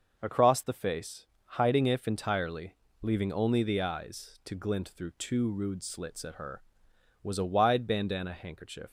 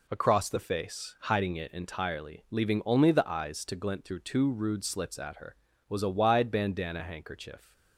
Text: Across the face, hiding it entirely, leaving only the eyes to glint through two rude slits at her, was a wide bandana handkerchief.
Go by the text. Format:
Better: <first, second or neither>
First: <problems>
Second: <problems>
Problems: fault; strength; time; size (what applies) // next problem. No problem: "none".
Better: second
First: says "if" for "it"; at 1.8 s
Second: none